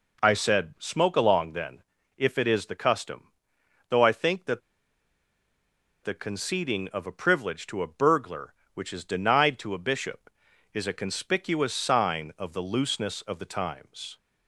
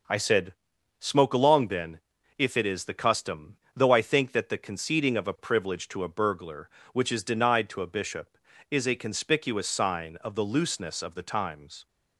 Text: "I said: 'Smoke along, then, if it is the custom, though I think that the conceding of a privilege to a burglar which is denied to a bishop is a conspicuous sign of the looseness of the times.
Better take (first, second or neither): second